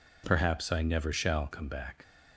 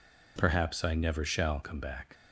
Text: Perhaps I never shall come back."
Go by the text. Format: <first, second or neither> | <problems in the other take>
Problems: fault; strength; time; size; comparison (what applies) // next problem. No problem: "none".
neither | none